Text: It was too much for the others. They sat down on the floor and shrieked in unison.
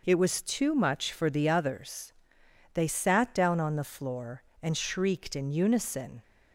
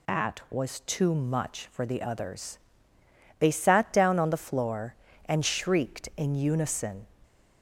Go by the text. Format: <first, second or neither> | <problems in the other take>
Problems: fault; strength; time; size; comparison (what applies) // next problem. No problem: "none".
first | says "At" for "It"; at 0.0 s